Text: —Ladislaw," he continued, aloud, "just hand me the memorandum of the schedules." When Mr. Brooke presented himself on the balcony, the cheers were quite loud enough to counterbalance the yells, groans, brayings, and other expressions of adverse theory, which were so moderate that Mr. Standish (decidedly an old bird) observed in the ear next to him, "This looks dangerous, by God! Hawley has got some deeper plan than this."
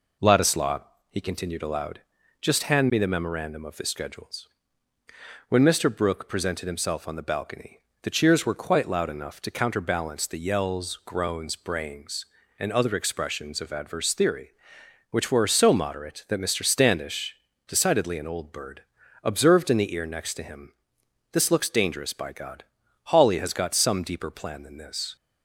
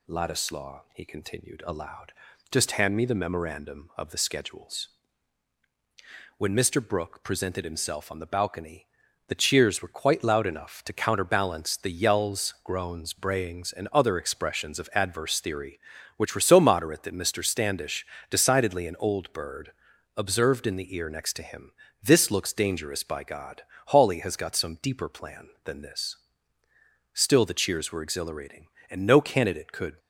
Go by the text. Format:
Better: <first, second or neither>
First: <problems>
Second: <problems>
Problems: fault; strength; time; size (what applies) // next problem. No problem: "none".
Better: first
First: none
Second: goes on to say "Still the cheers were exhilarating and no candidate could"; strong; from 27.1 s on; 2.8 s long